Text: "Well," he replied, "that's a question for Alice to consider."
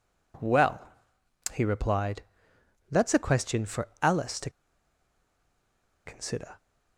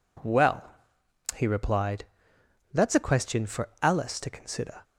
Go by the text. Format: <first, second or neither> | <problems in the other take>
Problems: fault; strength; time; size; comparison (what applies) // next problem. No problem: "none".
second | pauses between "to" and "consider"; strong; at 4.4 s; 1.5 s long